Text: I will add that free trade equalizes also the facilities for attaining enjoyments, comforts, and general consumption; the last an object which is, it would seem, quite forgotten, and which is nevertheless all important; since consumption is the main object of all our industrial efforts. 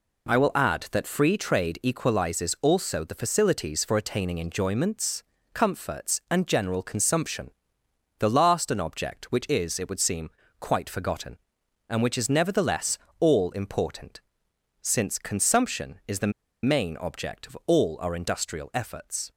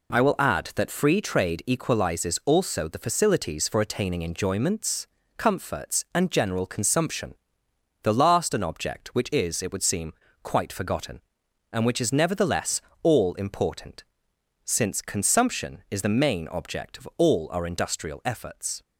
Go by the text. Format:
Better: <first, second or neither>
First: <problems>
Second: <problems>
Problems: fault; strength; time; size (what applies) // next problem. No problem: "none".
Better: second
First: pauses between "nevertheless" and "all"; slight; at 12.9 s; 0.22 s long // pauses between "the" and "main"; slight; at 16.3 s; 0.33 s long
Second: pauses between "nevertheless" and "all"; slight; at 12.8 s; 0.22 s long